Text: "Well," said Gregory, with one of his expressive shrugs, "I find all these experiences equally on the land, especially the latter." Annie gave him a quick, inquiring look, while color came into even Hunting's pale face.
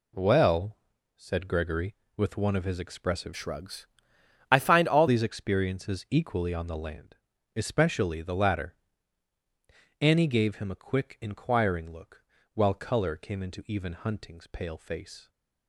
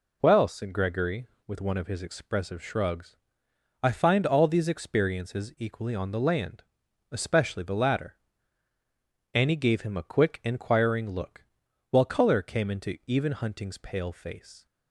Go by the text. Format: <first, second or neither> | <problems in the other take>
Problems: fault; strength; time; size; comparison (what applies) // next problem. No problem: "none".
second | changes voice from "shrugs" to "all"; from 3.3 to 5.0 s; 1.7 s long